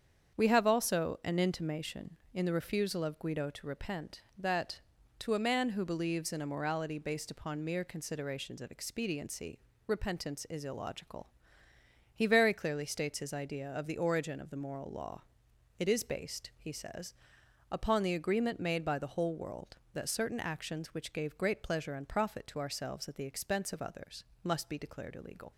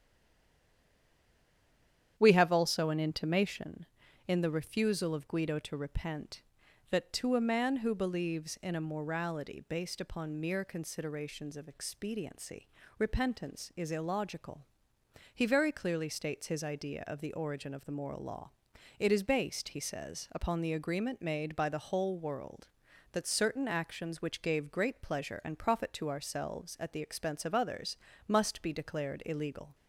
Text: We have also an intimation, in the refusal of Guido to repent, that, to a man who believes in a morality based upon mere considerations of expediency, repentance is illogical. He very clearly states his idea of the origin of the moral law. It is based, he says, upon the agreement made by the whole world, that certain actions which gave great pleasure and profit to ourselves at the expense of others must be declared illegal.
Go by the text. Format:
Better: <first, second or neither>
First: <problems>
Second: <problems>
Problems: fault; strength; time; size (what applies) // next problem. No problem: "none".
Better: first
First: starts louder than the rest; strong; until 1.4 s; 7.5 dB // pauses between "others" and "must"; slight; at 24.2 s; 0.20 s long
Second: stays silent before the first word; until 2.1 s; 2.1 s long // starts louder than the rest; strong; until 3.1 s; 9.5 dB // pauses between "others" and "must"; slight; at 27.9 s; 0.32 s long